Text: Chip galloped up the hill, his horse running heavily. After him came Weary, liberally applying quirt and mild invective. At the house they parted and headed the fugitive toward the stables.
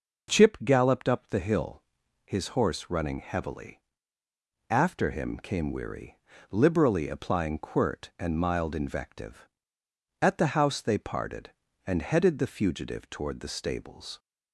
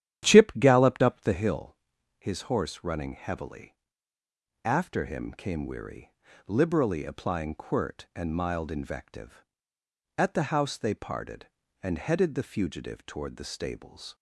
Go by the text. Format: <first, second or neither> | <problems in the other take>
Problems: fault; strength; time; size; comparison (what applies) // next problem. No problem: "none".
first | starts louder than the rest; strong; until 1.6 s; 10.5 dB